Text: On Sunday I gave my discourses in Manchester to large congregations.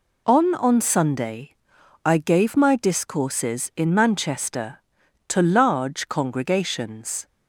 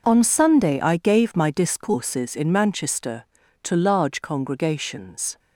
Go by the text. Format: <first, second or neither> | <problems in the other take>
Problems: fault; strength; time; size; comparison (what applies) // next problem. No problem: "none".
second | says "On" twice; at 0.5 s // pauses between "Sunday" and "I"; noticeable; at 1.5 s; 0.50 s long